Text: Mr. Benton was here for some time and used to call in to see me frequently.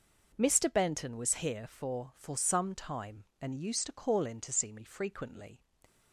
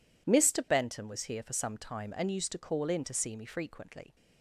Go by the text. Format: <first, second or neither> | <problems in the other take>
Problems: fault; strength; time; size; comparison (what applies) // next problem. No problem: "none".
second | says "for" twice; at 2.1 s